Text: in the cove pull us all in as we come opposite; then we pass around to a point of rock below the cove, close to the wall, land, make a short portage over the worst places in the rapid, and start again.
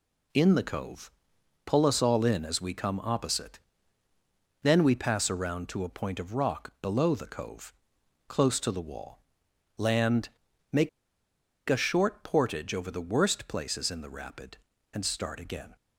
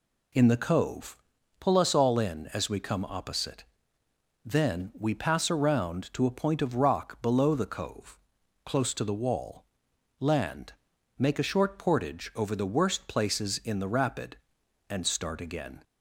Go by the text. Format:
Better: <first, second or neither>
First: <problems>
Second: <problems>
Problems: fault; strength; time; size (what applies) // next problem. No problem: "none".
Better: second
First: pauses between "cove" and "pull"; noticeable; at 1.1 s; 0.54 s long // pauses between "make" and "a"; noticeable; at 10.8 s; 0.79 s long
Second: pauses between "cove" and "pull"; at 1.1 s; 0.43 s long